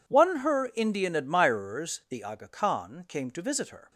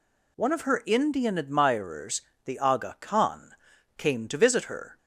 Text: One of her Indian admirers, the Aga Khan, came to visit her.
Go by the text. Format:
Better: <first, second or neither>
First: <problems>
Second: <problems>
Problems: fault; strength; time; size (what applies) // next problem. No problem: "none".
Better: second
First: skips "of"; at 0.3 s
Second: none